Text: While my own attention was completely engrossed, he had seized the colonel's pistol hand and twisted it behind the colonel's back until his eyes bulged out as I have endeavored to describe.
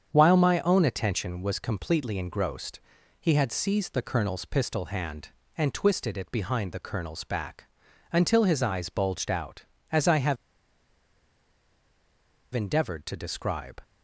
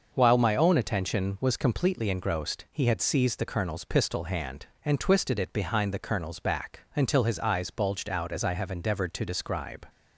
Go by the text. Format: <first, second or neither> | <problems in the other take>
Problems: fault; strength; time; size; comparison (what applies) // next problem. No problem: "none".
second | starts louder than the rest; strong; until 1.1 s; 7.5 dB; noticeable in the second // pauses between "back" and "until"; noticeable; at 7.6 s; 0.48 s long; slight in the second // pauses between "have" and "endeavored"; strong; at 10.3 s; 2.1 s long